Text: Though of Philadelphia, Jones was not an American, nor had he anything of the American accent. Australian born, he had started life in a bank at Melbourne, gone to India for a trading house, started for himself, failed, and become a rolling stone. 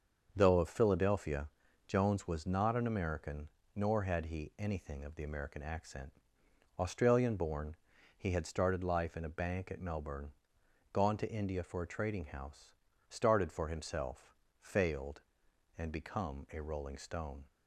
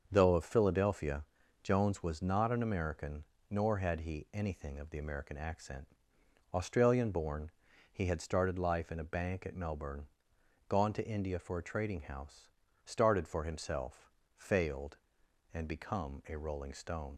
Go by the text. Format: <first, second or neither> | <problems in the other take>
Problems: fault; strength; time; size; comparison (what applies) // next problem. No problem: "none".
first | starts louder than the rest; until 1.1 s; 6.5 dB; also in the first // leaves "stone" unfinished; at 17.1 s; 60 ms